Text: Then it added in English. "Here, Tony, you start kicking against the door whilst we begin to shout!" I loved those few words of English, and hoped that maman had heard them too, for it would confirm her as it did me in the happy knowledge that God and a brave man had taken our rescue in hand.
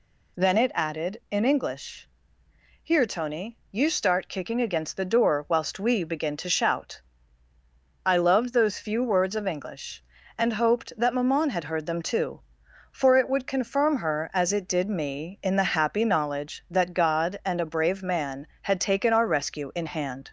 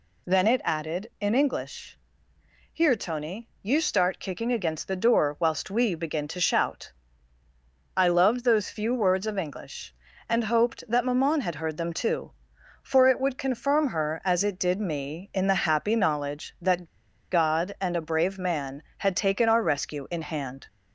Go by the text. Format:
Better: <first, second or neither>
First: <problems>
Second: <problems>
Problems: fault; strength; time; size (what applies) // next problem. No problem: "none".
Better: first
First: none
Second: pauses between "that" and "God"; at 16.8 s; 0.45 s long